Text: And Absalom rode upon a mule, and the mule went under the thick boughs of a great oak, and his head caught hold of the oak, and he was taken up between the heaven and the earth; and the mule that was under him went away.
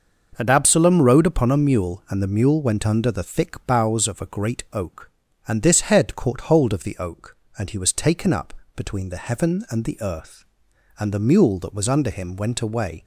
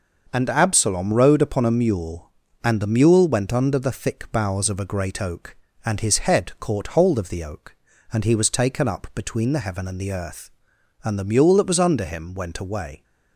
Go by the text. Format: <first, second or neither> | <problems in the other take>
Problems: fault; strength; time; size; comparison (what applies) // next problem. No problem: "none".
second | starts louder than the rest; noticeable; until 1.3 s; 6 dB; noticeable in the second // says "this" for "his"; at 5.6 s // pauses between "up" and "between"; slight; at 8.5 s; 0.24 s long